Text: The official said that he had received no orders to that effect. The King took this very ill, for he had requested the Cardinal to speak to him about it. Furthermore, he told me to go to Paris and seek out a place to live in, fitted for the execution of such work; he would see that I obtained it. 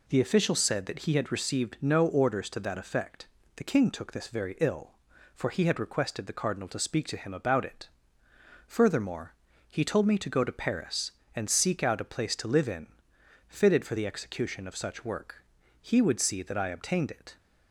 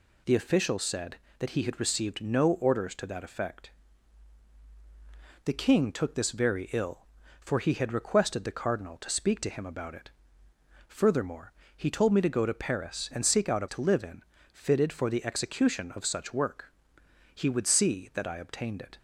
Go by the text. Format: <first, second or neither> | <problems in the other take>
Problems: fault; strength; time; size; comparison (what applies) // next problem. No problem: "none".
first | skips "place"; at 13.6 s